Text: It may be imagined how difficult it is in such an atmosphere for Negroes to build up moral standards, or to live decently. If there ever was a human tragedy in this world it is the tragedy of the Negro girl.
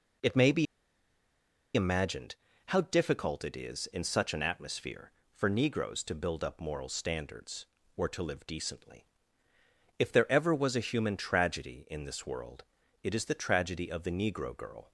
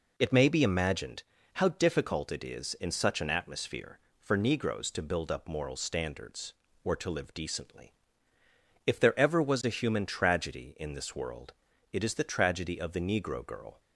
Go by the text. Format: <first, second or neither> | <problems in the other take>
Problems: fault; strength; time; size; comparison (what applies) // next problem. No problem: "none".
second | pauses between "be" and "imagined"; at 0.6 s; 1.0 s long // pauses between "imagined" and "how"; slight; at 2.3 s; 0.32 s long; slight in the second // pauses between "world" and "it"; at 12.6 s; 0.40 s long; also in the second